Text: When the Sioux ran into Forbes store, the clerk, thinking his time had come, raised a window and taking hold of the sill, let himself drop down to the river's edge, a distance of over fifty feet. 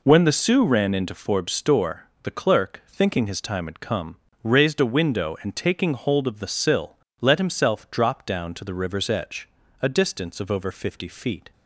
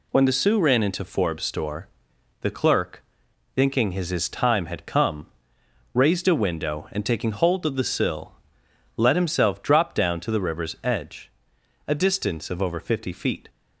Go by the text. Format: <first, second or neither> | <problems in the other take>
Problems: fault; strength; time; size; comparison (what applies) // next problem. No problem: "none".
first | says "his" twice; at 4.0 s